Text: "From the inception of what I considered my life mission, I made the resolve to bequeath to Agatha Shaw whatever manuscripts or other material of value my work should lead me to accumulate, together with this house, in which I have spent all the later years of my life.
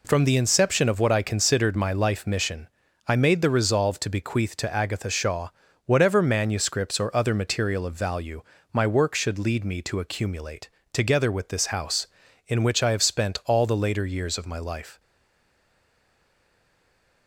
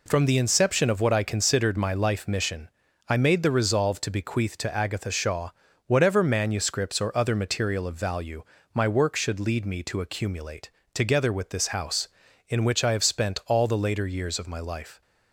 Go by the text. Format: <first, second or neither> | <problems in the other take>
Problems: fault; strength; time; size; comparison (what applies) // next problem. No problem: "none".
second | pauses between "Shaw" and "whatever"; at 5.4 s; 0.38 s long; also in the second // pauses between "value" and "my"; slight; at 8.4 s; 0.30 s long; slight in the second // stays silent after the last word; from 14.9 s on; 2.3 s long